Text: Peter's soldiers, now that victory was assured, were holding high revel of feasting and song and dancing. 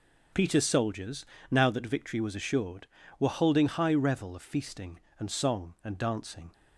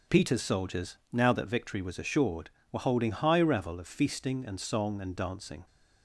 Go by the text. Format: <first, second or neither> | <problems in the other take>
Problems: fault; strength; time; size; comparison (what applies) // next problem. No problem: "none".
neither | none